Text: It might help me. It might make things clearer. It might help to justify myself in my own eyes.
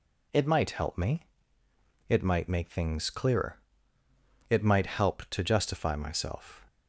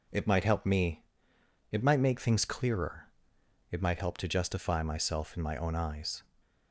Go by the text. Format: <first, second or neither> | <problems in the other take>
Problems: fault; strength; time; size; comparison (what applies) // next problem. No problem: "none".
second | stops before "in my own eyes"; at 6.6 s